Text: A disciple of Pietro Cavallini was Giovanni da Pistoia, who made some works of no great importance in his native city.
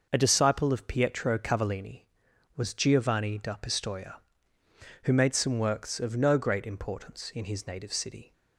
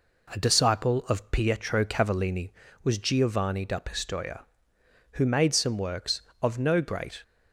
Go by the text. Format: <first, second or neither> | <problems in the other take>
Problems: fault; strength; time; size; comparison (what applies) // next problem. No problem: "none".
first | stops before "importance in his native city"; at 7.2 s